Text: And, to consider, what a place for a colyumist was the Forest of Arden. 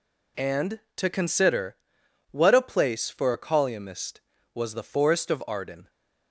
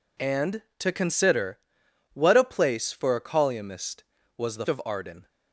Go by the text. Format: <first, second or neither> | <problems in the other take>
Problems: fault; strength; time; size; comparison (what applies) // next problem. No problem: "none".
first | skips "Forest"; at 4.6 s